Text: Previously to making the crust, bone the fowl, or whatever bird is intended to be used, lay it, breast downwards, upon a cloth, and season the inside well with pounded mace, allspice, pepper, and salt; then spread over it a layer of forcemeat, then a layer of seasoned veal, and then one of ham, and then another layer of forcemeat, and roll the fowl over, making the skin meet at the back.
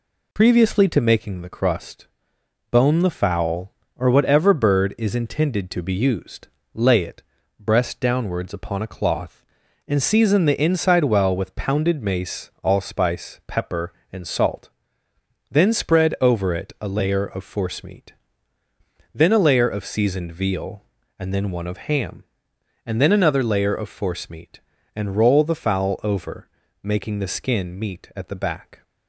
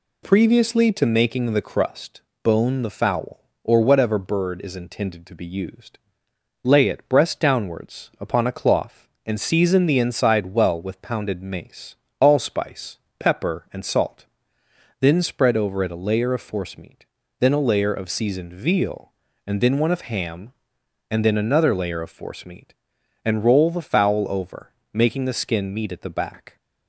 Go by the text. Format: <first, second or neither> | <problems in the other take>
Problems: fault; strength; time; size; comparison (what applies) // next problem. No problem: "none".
neither | none